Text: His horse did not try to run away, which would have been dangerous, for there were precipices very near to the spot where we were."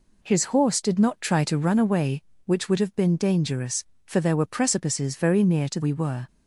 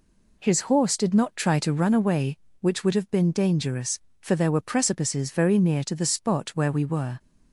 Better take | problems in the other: second | skips "the spot where"; at 5.8 s

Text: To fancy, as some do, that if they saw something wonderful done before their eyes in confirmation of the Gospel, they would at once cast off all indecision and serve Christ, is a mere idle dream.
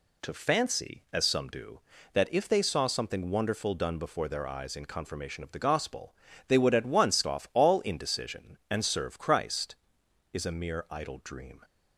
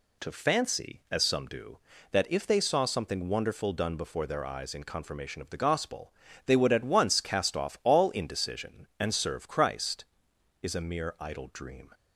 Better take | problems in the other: second | skips "cast"; at 7.2 s

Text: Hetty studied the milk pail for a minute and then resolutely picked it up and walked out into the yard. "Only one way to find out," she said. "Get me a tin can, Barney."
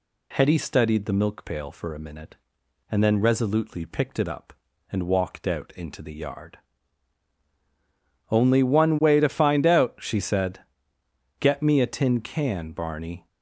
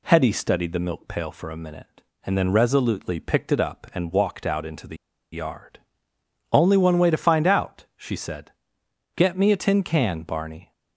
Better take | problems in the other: first | pauses between "the" and "yard"; at 4.9 s; 0.37 s long

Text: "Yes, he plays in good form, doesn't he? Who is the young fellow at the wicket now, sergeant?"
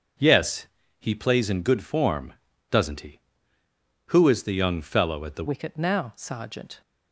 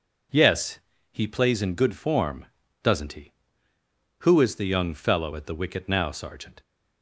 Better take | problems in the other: second | changes voice at "wicket"; from 5.4 s on; 1.4 s long

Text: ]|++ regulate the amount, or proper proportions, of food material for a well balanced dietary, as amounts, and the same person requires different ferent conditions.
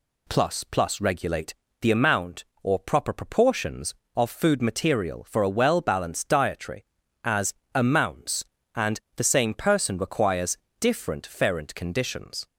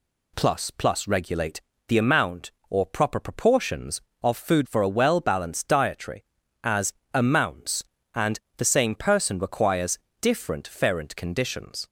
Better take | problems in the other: first | pauses between "regulate" and "the"; slight; at 1.6 s; 0.28 s long; slight in the first // skips "material"; at 4.6 s // pauses between "as" and "amounts"; slight; at 6.9 s; 0.20 s long; slight in the first // pauses between "and" and "the"; slight; at 8.3 s; 0.18 s long; slight in the first // pauses between "requires" and "different"; slight; at 9.9 s; 0.24 s long; slight in the first

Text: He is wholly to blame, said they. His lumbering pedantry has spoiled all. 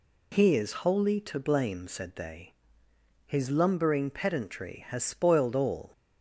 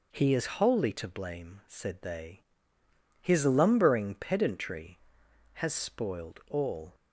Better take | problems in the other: neither | none

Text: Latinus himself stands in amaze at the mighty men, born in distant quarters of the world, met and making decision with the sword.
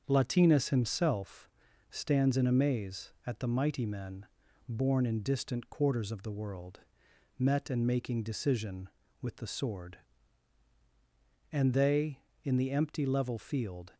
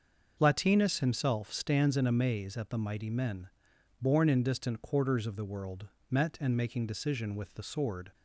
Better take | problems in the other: second | starts louder than the rest; until 1.0 s; 7 dB; also in the second // pauses between "himself" and "stands"; at 1.4 s; 0.42 s long // goes on to say "And they in the empty level field"; strong; from 11.5 s on; 2.4 s long

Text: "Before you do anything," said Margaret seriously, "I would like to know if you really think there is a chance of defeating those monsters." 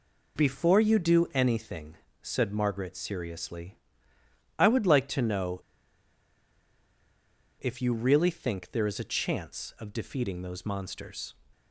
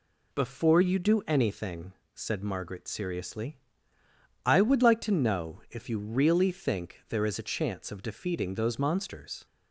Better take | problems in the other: second | pauses between "know" and "if"; strong; at 5.6 s; 1.9 s long

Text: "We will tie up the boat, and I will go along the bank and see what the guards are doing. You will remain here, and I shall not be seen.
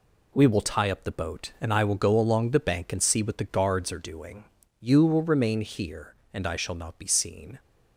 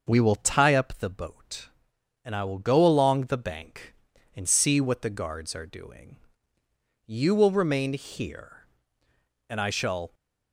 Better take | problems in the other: first | starts louder than the rest; noticeable; until 1.0 s; 6 dB // stops before "not be seen"; at 10.1 s

